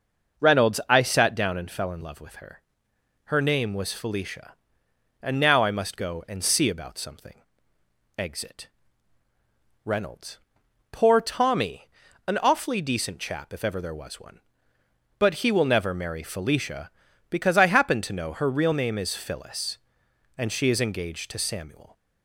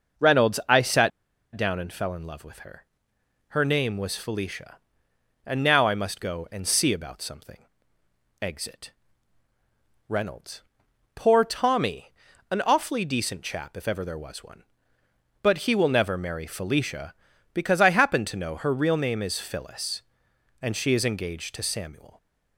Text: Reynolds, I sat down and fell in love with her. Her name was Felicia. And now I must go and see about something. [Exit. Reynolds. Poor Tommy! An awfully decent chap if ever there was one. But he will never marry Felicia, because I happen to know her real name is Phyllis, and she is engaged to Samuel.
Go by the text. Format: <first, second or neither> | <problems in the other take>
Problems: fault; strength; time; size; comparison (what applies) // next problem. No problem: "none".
first | pauses between "sat" and "down"; at 1.1 s; 0.44 s long